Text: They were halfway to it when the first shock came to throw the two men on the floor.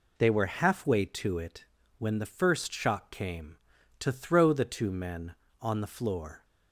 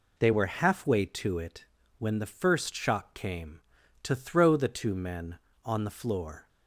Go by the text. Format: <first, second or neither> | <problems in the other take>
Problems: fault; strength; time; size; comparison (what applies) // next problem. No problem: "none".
neither | pauses between "it" and "when"; slight; the same in both